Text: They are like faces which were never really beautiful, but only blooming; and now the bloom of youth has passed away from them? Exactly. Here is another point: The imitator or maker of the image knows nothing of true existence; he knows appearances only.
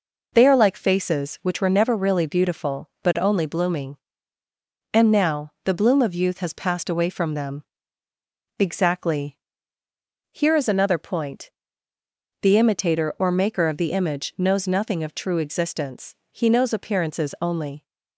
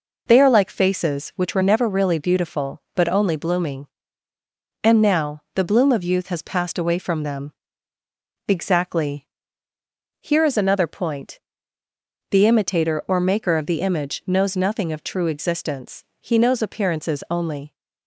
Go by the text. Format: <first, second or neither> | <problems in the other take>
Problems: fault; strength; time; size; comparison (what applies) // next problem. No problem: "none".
neither | none